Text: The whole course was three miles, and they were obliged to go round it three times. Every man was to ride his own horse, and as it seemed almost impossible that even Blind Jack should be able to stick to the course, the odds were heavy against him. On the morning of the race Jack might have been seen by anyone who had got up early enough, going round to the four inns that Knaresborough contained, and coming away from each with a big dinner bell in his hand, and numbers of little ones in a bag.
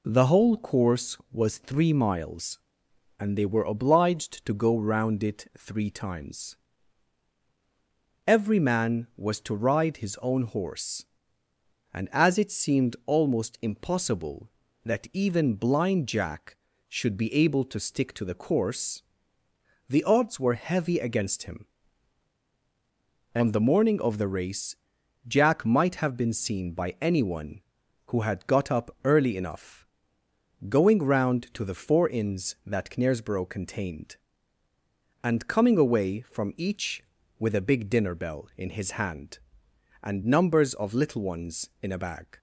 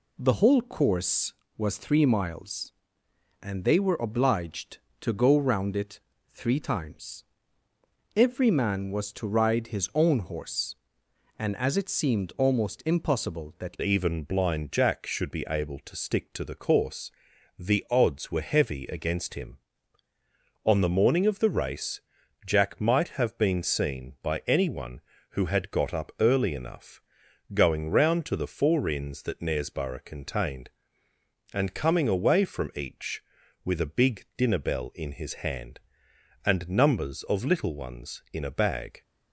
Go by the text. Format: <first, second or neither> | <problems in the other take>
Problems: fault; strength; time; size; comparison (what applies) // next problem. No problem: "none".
first | pauses between "it" and "three"; slight; at 5.9 s; 0.34 s long // changes voice at "even"; from 13.8 s on; 25.2 s long // pauses between "race" and "Jack"; at 21.9 s; 0.44 s long; noticeable in the first